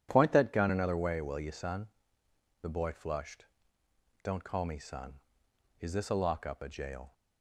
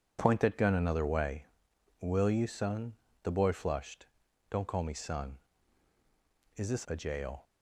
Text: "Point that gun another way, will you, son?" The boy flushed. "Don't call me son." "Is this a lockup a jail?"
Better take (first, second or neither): first